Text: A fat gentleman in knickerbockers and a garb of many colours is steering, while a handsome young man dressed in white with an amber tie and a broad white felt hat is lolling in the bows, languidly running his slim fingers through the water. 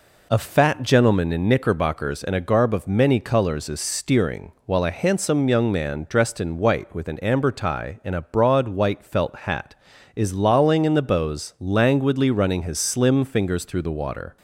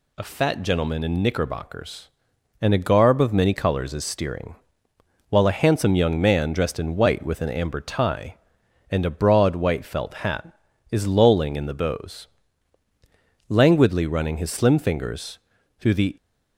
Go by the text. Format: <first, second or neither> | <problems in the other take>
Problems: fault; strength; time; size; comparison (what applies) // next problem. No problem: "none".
first | pauses between "fingers" and "through"; at 15.3 s; 0.40 s long // stops before "water"; at 16.1 s